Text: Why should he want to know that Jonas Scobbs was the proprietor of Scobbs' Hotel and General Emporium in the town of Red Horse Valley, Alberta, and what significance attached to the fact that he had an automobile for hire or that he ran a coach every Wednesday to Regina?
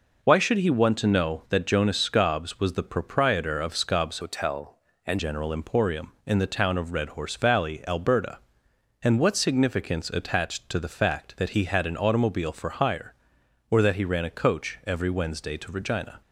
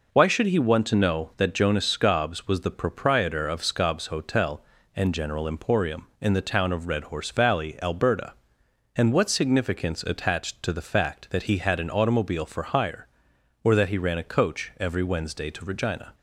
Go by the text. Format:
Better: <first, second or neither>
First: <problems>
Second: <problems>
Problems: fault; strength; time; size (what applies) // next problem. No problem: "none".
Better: second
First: changes voice from "Hotel" to "and"; from 4.2 to 5.1 s; 0.9 s long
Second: none